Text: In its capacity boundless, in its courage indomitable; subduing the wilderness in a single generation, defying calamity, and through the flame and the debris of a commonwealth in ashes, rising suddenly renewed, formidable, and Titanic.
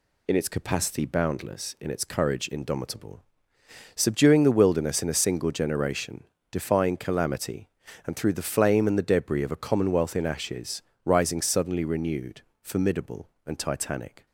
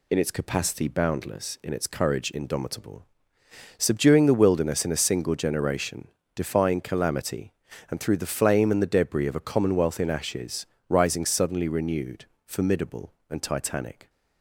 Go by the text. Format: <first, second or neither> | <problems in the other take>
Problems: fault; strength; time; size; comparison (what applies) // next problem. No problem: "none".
neither | none